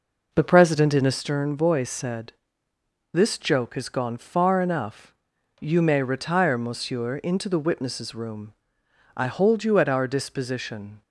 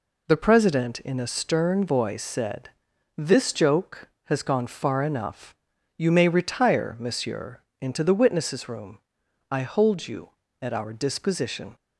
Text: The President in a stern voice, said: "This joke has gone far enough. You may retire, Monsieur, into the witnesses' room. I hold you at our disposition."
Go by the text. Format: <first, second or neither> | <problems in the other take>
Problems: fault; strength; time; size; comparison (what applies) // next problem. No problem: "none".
second | starts louder than the rest; noticeable; until 1.2 s; 5 dB